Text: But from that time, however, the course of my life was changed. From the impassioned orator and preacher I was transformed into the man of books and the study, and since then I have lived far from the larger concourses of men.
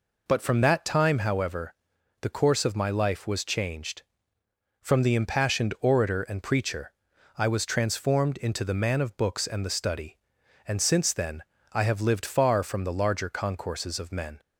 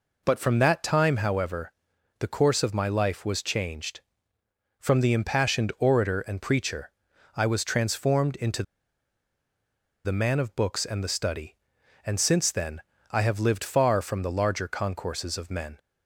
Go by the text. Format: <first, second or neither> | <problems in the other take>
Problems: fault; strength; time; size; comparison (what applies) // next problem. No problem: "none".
first | pauses between "preacher" and "I"; noticeable; at 6.9 s; 0.46 s long; noticeable in the first // pauses between "into" and "the"; strong; at 8.6 s; 1.4 s long // pauses between "then" and "I"; slight; at 12.7 s; 0.32 s long; slight in the first